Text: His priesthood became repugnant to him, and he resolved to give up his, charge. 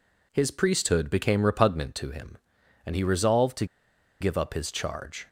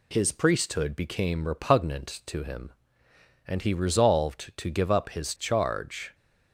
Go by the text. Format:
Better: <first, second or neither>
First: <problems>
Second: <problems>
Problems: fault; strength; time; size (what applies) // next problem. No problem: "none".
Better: second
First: pauses between "to" and "give"; noticeable; at 3.6 s; 0.55 s long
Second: none